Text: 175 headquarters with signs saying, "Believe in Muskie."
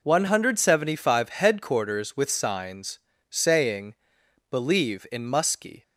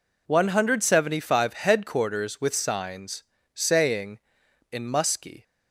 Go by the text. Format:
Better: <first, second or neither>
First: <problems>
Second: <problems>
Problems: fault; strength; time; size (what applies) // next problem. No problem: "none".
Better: first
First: pauses between "signs" and "saying"; slight; at 2.9 s; 0.32 s long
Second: pauses between "signs" and "saying"; slight; at 3.2 s; 0.32 s long // skips "Believe"; at 4.4 s